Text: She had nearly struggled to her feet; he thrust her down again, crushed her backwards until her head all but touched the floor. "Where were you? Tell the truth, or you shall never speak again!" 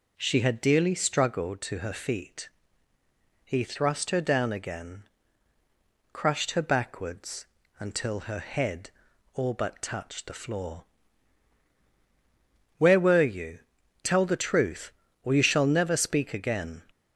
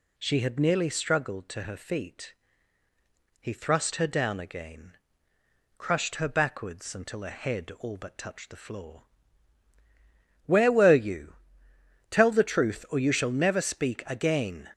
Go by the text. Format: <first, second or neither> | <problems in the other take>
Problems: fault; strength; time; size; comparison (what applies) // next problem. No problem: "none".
second | says "dearly" for "nearly"; at 0.6 s // pauses between "backwards" and "until"; slight; at 7.4 s; 0.34 s long // pauses between "head" and "all"; noticeable; at 8.8 s; 0.46 s long